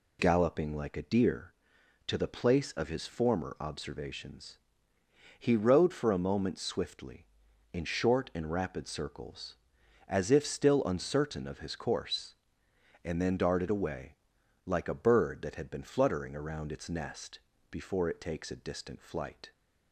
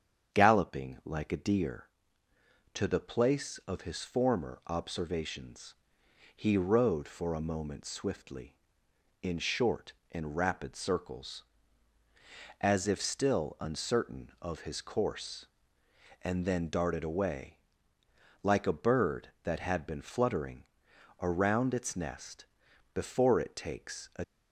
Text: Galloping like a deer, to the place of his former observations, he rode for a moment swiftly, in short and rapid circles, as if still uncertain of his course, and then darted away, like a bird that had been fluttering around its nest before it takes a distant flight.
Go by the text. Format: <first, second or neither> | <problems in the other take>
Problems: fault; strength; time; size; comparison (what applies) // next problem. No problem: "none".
first | starts louder than the rest; strong; until 1.4 s; 8 dB // pauses between "fluttering" and "around"; noticeable; at 20.6 s; 0.58 s long // pauses between "nest" and "before"; noticeable; at 22.4 s; 0.48 s long; slight in the first // stops before "distant flight"; at 24.2 s